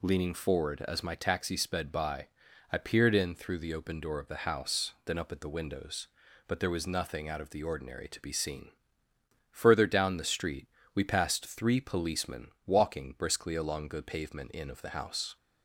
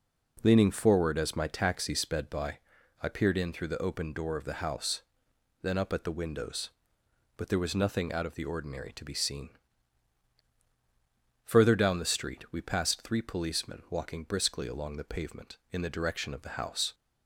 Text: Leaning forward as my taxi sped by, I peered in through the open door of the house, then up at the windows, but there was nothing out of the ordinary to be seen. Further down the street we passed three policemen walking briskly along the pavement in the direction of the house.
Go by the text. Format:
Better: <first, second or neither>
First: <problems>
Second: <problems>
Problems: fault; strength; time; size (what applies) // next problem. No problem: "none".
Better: second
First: pauses between "street" and "we"; slight; at 10.6 s; 0.26 s long // pauses between "policemen" and "walking"; slight; at 12.4 s; 0.18 s long // skips "the direction"; at 14.7 s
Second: none